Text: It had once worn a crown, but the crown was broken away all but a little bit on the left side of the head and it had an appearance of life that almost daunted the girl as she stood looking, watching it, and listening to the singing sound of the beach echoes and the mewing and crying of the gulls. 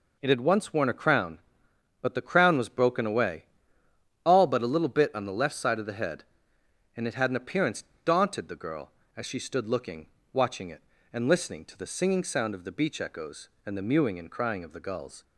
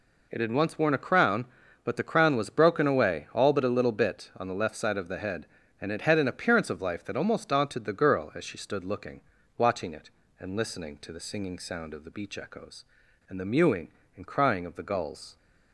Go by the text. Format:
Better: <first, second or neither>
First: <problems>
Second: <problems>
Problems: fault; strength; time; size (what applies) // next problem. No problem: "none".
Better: second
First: pauses between "away" and "all"; noticeable; at 3.4 s; 0.82 s long // skips "of life that almost"; at 7.9 s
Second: none